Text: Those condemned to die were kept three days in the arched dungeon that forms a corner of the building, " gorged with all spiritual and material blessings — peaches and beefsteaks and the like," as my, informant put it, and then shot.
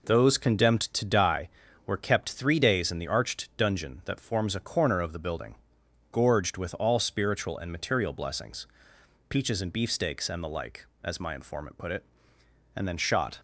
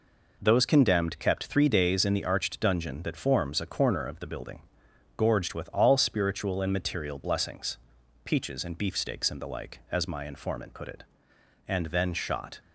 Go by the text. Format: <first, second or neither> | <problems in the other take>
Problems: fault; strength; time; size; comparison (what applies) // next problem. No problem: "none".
first | skips "to die were"; at 1.1 s